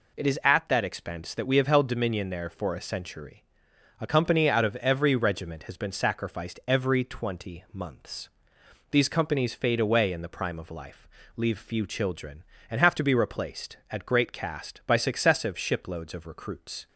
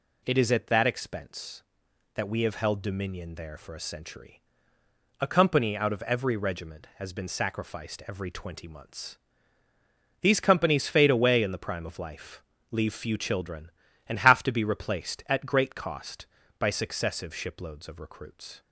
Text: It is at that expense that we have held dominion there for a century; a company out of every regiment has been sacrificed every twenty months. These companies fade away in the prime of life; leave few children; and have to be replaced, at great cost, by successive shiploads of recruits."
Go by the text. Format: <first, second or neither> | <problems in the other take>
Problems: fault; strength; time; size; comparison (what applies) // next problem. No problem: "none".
second | says "cast" for "cost"; at 14.3 s